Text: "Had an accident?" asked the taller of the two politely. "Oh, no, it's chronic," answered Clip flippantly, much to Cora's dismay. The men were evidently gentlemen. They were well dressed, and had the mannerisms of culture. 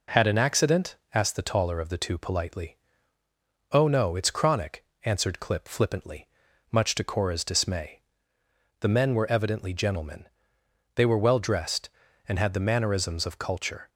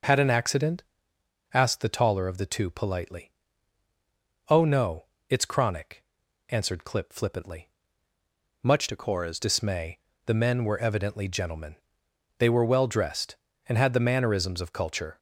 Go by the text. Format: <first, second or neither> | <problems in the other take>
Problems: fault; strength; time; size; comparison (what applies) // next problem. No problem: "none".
first | changes voice from "to" to "Cora's"; from 8.8 to 9.3 s; 0.5 s long